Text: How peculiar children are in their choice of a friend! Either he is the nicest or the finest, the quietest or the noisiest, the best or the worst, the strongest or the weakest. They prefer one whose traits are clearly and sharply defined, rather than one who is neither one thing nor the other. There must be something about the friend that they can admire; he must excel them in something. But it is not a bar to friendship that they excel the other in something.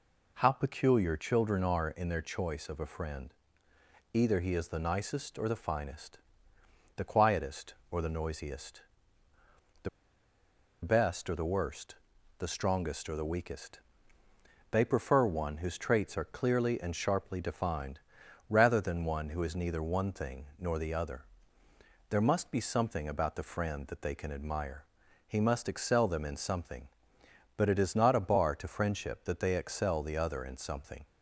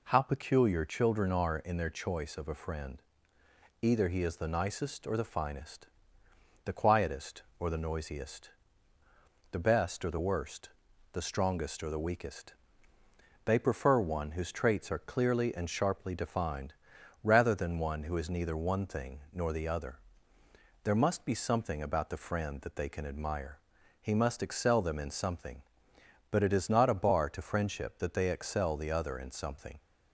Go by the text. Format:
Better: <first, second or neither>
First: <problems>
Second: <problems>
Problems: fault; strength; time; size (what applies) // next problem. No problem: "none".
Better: second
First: pauses between "the" and "best"; noticeable; at 9.8 s; 0.93 s long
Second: none